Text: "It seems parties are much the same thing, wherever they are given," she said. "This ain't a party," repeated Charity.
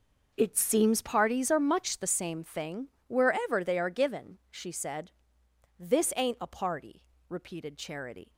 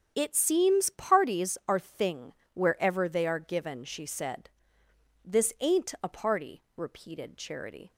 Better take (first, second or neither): first